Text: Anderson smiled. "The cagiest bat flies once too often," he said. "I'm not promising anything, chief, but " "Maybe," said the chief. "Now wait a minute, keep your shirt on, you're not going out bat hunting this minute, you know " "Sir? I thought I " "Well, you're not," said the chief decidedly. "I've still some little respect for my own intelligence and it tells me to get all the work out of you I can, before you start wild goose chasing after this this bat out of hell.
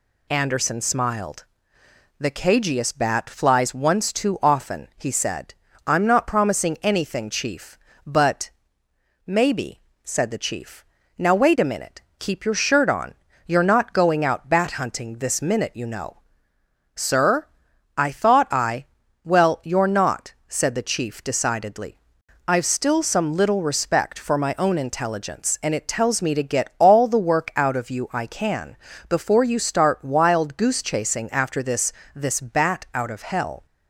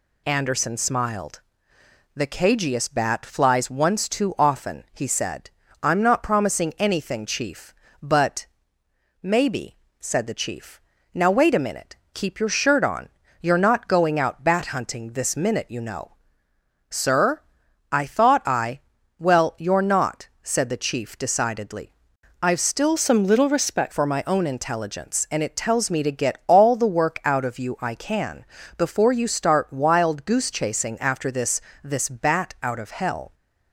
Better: first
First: pauses between "this" and "this"; slight; at 31.9 s; 0.24 s long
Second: changes voice from "some" to "respect"; from 22.9 to 23.9 s; 1.0 s long // pauses between "this" and "this"; slight; at 31.5 s; 0.24 s long

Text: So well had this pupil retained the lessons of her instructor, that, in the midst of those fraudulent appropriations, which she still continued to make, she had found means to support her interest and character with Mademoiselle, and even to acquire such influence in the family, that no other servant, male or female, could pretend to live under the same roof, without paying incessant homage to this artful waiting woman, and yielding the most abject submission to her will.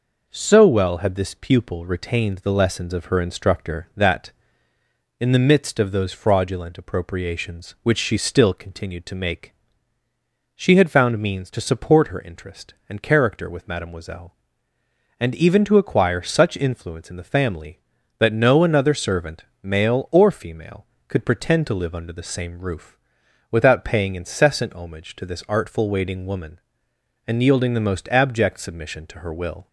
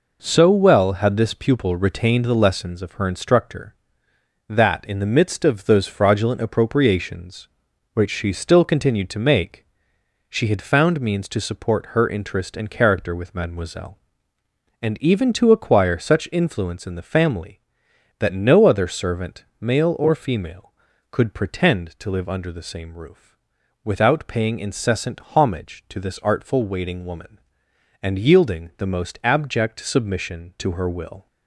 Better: second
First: says "another" for "other"; at 18.6 s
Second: none

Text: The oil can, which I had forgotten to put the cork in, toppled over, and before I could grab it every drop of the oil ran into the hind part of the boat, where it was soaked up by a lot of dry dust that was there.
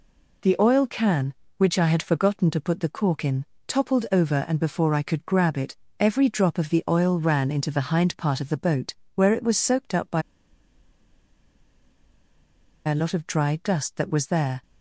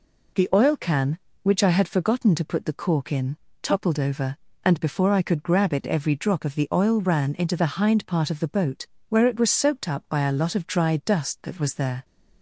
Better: second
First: pauses between "it" and "every"; slight; at 5.7 s; 0.22 s long // pauses between "by" and "a"; strong; at 10.2 s; 2.6 s long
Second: none

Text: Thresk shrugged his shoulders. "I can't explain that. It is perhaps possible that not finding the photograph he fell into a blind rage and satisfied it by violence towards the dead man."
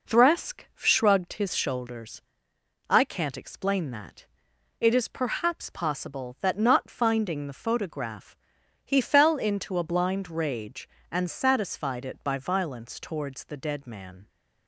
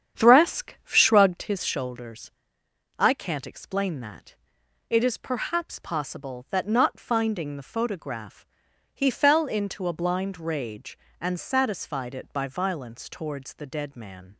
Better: first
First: pauses between "photograph" and "he"; noticeable; at 8.3 s; 0.48 s long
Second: starts louder than the rest; strong; until 1.6 s; 8.5 dB // pauses between "photograph" and "he"; noticeable; at 8.4 s; 0.48 s long

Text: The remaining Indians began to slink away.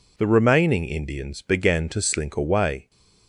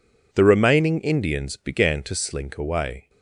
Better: neither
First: none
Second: none

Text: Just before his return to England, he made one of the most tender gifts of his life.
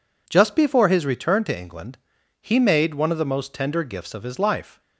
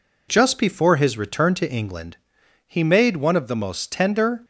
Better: first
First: none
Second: stops before "gifts of his life"; at 4.4 s

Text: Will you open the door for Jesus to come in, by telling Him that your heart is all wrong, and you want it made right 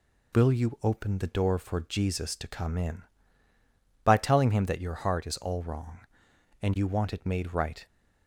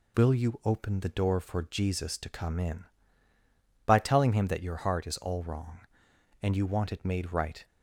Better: neither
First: none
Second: none

